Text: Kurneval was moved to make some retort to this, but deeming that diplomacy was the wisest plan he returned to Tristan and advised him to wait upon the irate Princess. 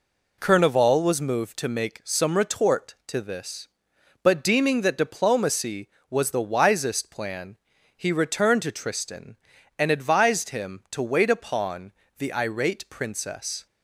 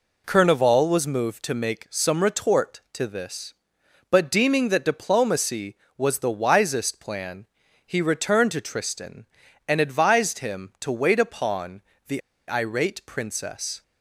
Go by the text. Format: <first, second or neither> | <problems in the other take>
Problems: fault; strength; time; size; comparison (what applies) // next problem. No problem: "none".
first | pauses between "plan" and "he"; at 7.4 s; 0.40 s long; also in the first // pauses between "upon" and "the"; slight; at 11.8 s; 0.26 s long; slight in the first // pauses between "the" and "irate"; slight; at 12.2 s; 0.29 s long